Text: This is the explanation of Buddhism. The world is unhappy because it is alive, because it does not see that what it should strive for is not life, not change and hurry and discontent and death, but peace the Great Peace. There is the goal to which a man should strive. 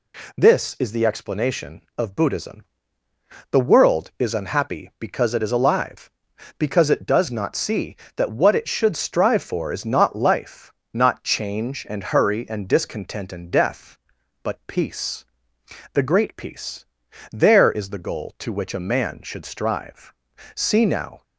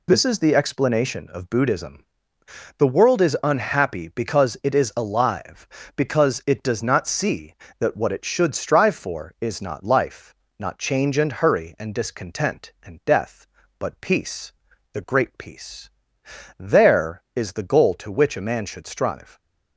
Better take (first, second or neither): second